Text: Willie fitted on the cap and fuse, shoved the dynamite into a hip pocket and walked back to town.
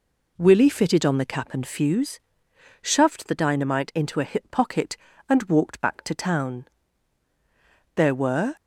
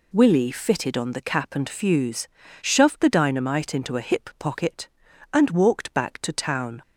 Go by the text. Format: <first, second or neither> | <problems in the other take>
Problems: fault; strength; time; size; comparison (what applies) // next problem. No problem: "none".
second | goes on to say "There were"; from 7.9 s on; 0.60 s long